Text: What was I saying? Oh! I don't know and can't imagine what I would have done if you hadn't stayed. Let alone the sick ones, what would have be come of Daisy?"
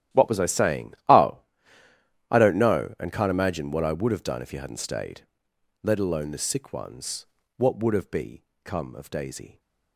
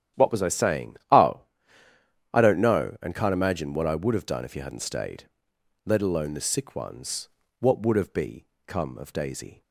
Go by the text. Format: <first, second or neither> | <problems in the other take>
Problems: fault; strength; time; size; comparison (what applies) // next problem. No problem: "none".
second | gets quieter; strong; throughout; 17.5 dB // starts louder than the rest; strong; until 1.2 s; 12 dB; strong in the second // pauses between "be" and "come"; slight; at 8.4 s; 0.20 s long; slight in the second